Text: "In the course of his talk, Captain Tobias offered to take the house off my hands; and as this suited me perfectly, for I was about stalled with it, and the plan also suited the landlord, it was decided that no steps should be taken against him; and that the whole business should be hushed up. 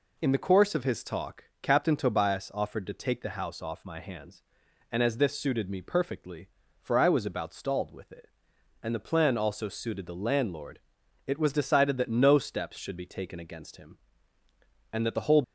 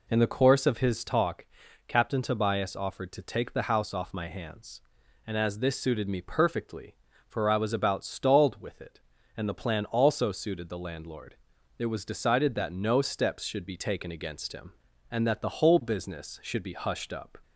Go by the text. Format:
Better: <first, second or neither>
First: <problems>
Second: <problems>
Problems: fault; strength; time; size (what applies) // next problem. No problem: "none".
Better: second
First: stops before "business should be hushed up"; at 15.4 s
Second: none